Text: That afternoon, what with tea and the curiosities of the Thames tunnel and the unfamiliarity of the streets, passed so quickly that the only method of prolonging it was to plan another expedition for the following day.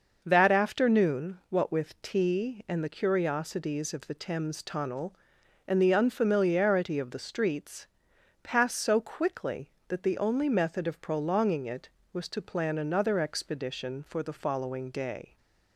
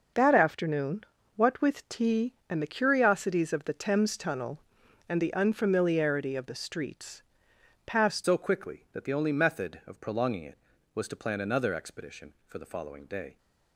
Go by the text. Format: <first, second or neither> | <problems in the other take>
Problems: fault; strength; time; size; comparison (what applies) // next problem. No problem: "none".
first | starts louder than the rest; until 1.4 s; 6 dB; noticeable in the first // changes voice at "so"; from 8.2 s on; 5.1 s long